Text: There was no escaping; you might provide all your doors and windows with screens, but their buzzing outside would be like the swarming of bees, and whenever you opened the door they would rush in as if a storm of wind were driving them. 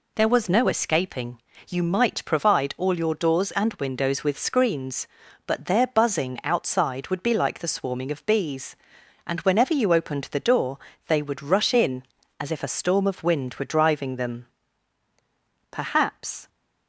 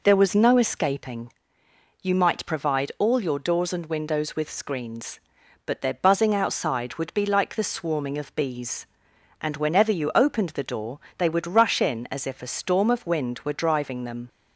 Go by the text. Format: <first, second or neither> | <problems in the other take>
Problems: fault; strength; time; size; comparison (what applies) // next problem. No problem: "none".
second | pauses between "door" and "they"; slight; at 10.7 s; 0.28 s long; slight in the second // goes on to say "Perhaps"; noticeable; from 15.6 s on; 0.78 s long